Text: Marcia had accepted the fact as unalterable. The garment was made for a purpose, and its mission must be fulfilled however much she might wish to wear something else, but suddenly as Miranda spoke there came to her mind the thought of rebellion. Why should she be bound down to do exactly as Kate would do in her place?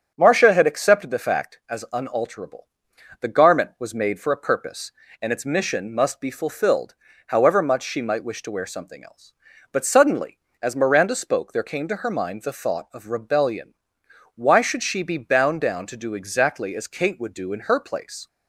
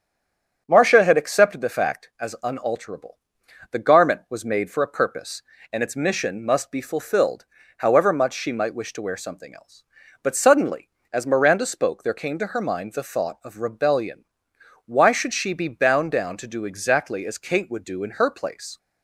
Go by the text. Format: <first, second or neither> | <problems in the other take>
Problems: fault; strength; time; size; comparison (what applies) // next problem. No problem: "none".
first | stays silent before the first word; slight; until 0.6 s; 0.6 s long // starts louder than the rest; strong; until 1.6 s; 8 dB; strong in the first // pauses between "fulfilled" and "however"; slight; at 7.4 s; 0.32 s long; slight in the first